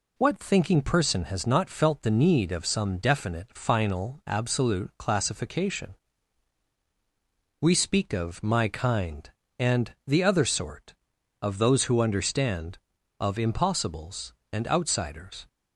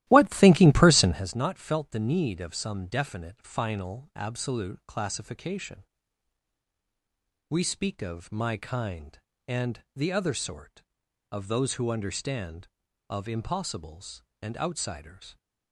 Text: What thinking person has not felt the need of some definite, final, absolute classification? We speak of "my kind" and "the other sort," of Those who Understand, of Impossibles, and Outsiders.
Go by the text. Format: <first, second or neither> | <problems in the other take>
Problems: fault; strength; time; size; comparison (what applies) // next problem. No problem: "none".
first | starts louder than the rest; strong; until 1.3 s; 14.5 dB